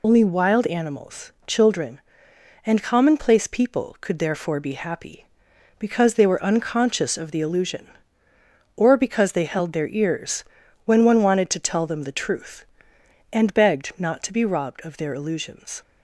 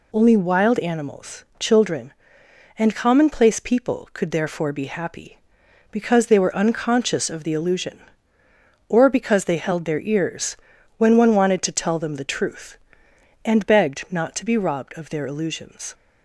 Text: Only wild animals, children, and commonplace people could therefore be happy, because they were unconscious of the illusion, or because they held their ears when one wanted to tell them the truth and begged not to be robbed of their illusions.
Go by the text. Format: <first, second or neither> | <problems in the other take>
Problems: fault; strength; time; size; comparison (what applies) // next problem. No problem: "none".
second | loses the start of "Only"; at 0.0 s; 30 ms // pauses between "ears" and "when"; at 10.4 s; 0.40 s long; also in the second